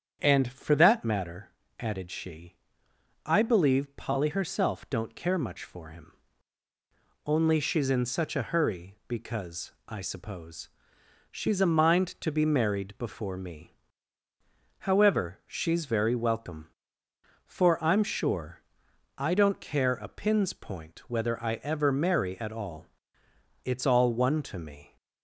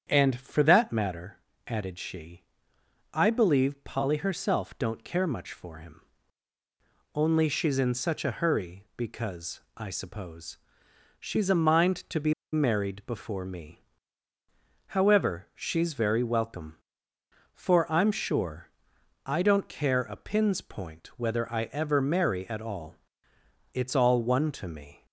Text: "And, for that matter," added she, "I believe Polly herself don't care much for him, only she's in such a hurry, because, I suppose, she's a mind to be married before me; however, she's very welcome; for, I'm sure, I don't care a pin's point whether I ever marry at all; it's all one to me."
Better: first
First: starts louder than the rest; strong; until 1.2 s; 8 dB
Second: starts louder than the rest; strong; until 1.1 s; 8 dB // pauses between "be" and "married"; slight; at 12.3 s; 0.19 s long

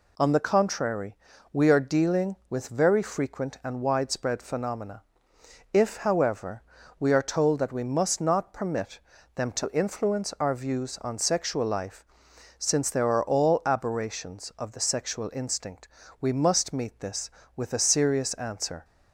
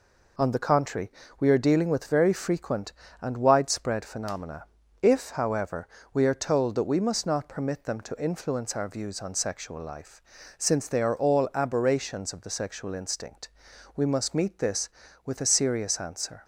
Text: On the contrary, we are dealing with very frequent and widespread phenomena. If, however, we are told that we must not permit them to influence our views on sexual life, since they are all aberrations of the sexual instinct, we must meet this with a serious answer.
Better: second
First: pauses between "permit" and "them"; at 8.9 s; 0.38 s long // says "there" for "they"; at 12.9 s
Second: none

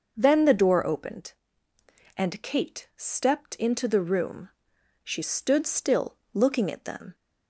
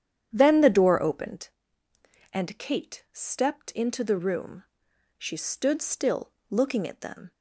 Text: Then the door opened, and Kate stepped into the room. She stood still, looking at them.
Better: first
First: none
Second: starts louder than the rest; strong; until 1.7 s; 9.5 dB

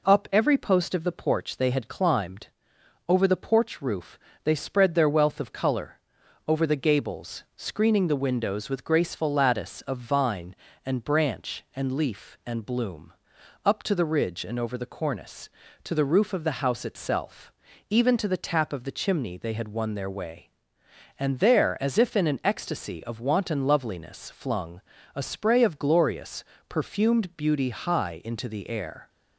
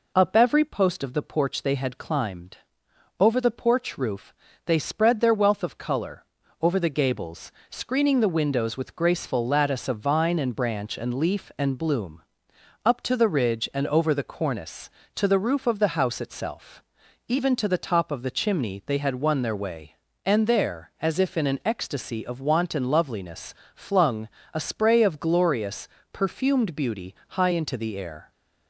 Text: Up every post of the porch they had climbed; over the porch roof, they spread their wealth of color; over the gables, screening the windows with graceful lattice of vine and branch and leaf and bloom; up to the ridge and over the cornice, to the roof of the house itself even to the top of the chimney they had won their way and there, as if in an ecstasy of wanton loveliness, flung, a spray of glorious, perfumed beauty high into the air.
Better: second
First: pauses between "itself" and "even"; slight; at 17.5 s; 0.36 s long // says "tap" for "top"; at 18.4 s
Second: pauses between "itself" and "even"; noticeable; at 16.8 s; 0.46 s long

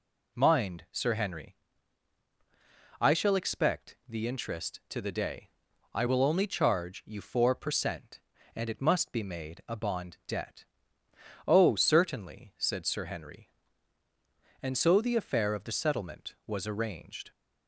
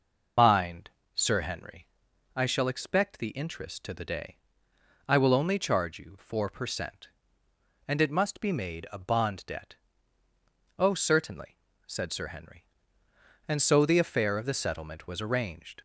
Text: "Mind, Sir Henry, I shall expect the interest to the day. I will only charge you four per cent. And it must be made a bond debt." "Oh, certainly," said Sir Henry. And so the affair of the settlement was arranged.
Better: first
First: none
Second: loses the start of "Mind"; at 0.3 s; 95 ms

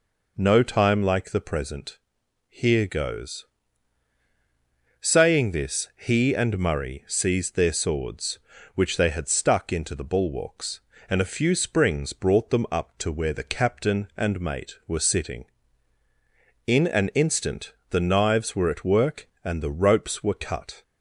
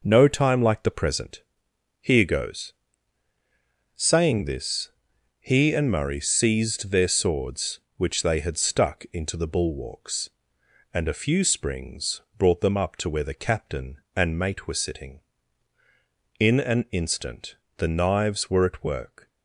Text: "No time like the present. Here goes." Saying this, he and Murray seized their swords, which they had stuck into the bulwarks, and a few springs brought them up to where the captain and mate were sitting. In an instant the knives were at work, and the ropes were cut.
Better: first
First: pauses between "instant" and "the"; slight; at 17.7 s; 0.18 s long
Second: pauses between "springs" and "brought"; slight; at 12.2 s; 0.16 s long // pauses between "instant" and "the"; slight; at 17.5 s; 0.22 s long // stops before "and the ropes were cut"; at 19.2 s

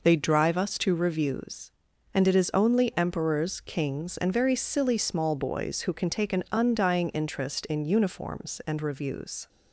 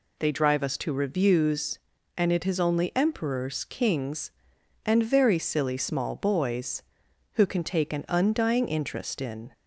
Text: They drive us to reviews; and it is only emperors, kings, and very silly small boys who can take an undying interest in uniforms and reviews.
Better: first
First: none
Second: stops before "uniforms and reviews"; at 9.5 s

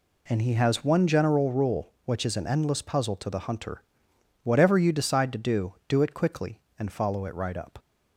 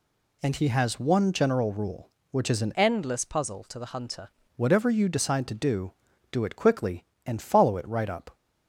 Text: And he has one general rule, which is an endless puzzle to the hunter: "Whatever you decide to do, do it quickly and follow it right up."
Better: first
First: none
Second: changes voice from "endless" to "hunter"; from 2.7 to 4.2 s; 1.5 s long

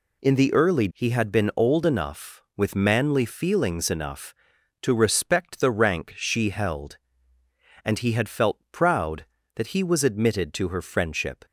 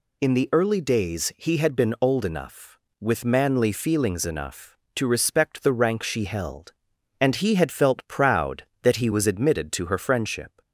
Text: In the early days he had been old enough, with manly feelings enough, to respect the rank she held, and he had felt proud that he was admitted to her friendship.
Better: second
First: skips "days"; at 0.8 s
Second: none

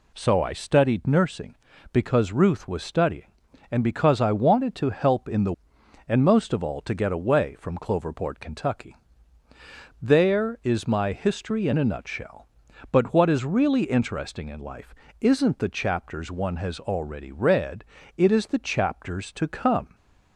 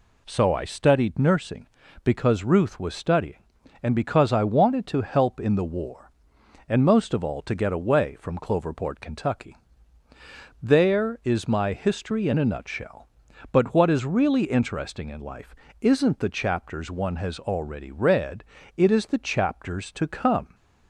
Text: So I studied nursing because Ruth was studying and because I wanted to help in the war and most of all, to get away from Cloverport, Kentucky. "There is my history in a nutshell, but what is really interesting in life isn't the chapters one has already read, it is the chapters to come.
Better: second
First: skips "war"; at 5.7 s // pauses between "life" and "isn't"; slight; at 14.9 s; 0.26 s long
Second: pauses between "life" and "isn't"; slight; at 15.5 s; 0.26 s long

